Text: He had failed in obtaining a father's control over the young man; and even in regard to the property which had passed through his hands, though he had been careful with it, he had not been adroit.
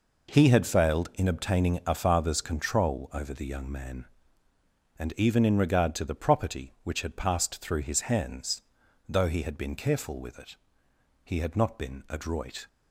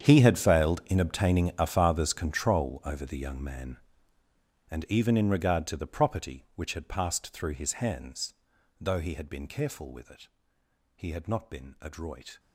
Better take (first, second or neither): first